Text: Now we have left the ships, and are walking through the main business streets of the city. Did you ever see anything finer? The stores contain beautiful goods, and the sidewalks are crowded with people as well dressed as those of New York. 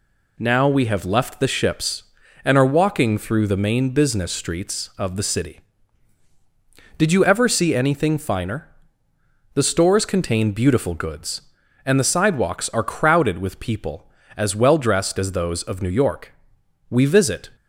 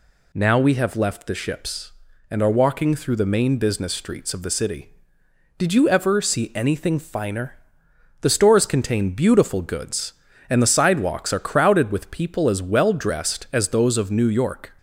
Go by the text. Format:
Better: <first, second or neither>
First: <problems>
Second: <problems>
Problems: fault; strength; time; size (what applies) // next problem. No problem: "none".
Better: second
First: goes on to say "We visit"; from 16.9 s on; 0.58 s long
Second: none